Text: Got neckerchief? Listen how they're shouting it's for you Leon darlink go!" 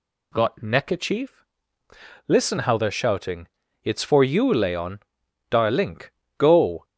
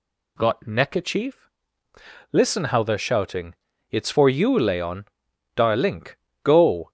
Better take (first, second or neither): neither